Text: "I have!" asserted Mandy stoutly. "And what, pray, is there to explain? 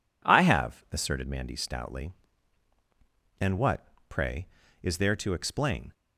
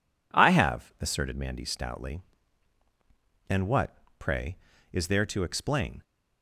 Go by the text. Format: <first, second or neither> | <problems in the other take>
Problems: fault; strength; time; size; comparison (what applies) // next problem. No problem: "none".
neither | none